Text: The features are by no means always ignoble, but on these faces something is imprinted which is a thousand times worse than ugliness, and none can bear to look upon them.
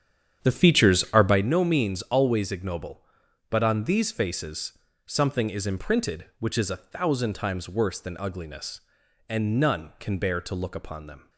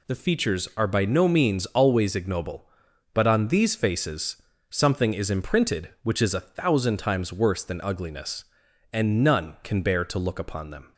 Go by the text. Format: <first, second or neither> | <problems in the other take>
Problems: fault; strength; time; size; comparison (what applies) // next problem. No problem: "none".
second | starts louder than the rest; strong; until 1.5 s; 9 dB // pauses between "faces" and "something"; slight; at 4.7 s; 0.28 s long; slight in the second